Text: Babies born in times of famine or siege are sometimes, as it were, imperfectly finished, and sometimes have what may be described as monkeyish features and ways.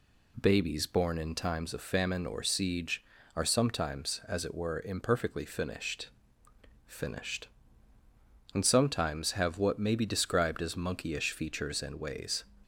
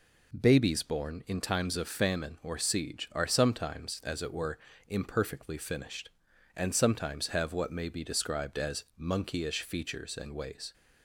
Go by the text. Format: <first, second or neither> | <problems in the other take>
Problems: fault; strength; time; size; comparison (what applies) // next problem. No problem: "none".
second | says "finished" twice; at 6.8 s